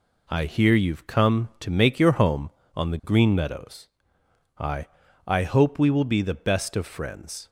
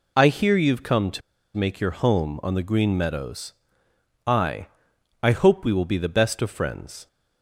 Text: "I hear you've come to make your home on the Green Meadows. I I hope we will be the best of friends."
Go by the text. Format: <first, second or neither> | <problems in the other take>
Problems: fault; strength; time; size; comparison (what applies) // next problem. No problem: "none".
first | pauses between "to" and "make"; slight; at 1.2 s; 0.36 s long // pauses between "I" and "I"; noticeable; at 4.6 s; 0.54 s long; also in the first